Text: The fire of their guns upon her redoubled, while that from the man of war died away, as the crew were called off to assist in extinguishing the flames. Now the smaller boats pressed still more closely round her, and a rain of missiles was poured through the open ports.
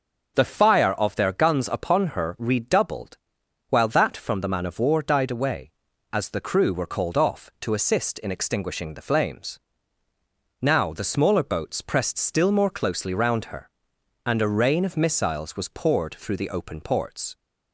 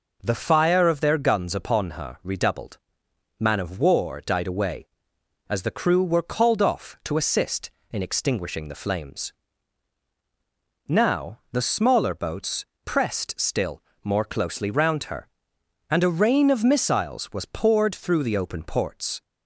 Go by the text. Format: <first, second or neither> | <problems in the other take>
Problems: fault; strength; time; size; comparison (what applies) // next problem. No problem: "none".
first | skips "while that from the"; at 3.0 s // pauses between "boats" and "pressed"; slight; at 12.6 s; 0.18 s long // pauses between "still" and "more"; slight; at 13.8 s; 0.22 s long